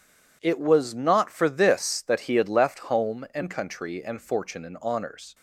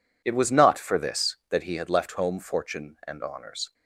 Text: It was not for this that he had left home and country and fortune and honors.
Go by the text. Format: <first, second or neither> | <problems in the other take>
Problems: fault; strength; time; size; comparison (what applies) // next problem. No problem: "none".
first | skips "and country and"; at 2.3 s